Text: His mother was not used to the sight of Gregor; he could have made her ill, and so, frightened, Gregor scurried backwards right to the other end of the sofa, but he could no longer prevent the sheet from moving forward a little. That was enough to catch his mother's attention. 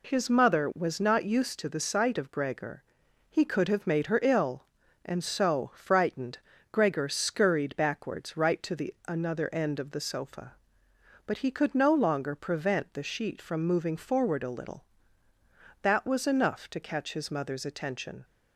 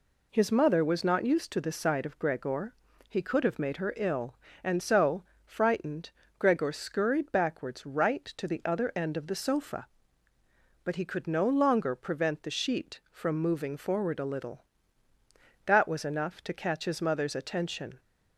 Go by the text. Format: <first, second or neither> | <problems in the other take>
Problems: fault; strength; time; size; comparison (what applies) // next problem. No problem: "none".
second | says "another" for "other"; at 9.0 s